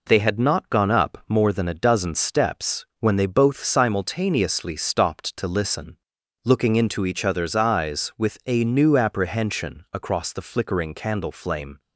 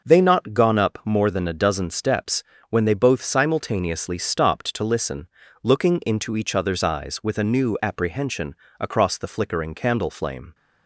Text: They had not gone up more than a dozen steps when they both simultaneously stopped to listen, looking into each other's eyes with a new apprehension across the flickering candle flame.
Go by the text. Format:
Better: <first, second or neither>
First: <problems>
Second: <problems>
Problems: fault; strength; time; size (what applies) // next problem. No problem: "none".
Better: first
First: pauses between "steps" and "when"; slight; at 2.8 s; 0.16 s long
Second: starts louder than the rest; noticeable; until 1.1 s; 6 dB // skips "had"; at 0.2 s // pauses between "steps" and "when"; slight; at 2.4 s; 0.28 s long // pauses between "apprehension" and "across"; slight; at 8.5 s; 0.24 s long